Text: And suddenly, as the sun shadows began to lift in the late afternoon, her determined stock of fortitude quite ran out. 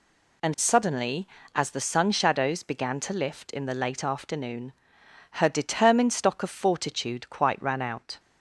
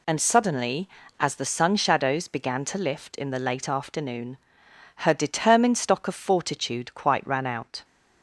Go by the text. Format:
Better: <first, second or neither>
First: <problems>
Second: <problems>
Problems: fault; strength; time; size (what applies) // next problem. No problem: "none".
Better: neither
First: none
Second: none